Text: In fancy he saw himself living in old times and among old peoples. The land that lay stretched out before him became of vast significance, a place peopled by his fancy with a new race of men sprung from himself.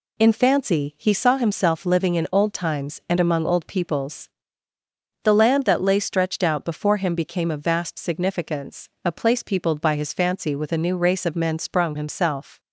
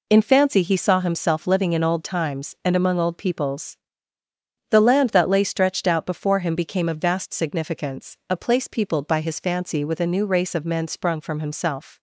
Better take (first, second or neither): second